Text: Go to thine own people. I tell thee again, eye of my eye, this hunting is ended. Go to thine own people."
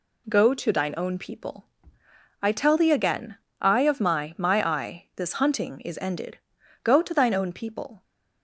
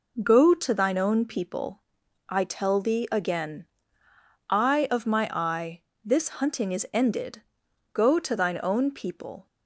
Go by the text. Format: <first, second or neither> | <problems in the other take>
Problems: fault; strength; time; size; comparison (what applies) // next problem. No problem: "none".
second | says "my" twice; at 4.3 s